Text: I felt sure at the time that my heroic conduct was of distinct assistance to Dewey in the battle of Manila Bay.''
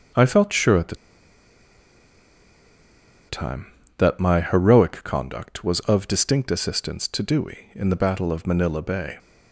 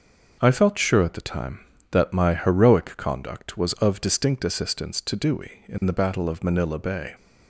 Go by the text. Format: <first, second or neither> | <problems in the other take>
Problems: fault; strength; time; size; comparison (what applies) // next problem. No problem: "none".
second | starts louder than the rest; noticeable; until 3.4 s; 6 dB; noticeable in the second // pauses between "the" and "time"; strong; at 0.9 s; 2.3 s long